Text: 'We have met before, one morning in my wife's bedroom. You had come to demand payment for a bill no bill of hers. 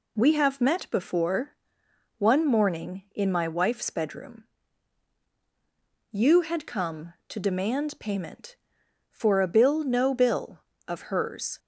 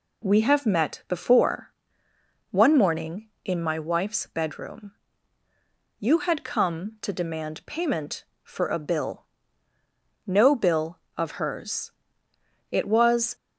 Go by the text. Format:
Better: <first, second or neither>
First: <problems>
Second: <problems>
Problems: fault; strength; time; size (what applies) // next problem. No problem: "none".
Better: first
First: none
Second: pauses between "bill" and "no"; at 9.2 s; 1.0 s long // goes on to say "It was"; noticeable; from 12.7 s on; 0.64 s long